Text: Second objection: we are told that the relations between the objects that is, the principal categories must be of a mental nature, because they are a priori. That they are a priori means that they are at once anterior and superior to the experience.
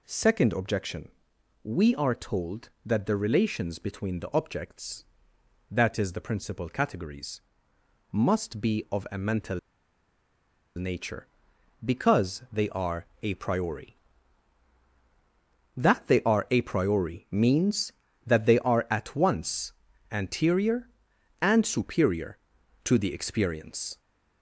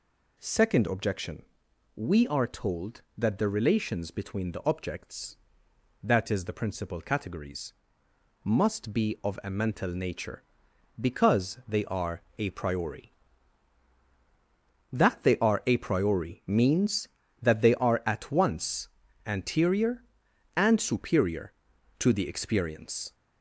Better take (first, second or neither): second